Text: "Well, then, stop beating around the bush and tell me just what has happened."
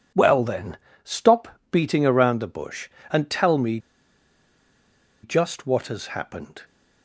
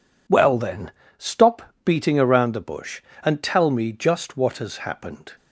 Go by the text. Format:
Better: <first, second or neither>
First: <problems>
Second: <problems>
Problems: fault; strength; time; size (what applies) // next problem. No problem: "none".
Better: second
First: pauses between "stop" and "beating"; slight; at 1.4 s; 0.24 s long // pauses between "me" and "just"; strong; at 3.7 s; 1.4 s long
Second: pauses between "stop" and "beating"; slight; at 1.6 s; 0.23 s long